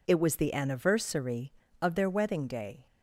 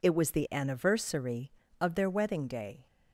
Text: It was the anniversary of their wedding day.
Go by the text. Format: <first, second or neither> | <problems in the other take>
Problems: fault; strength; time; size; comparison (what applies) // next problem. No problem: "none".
neither | none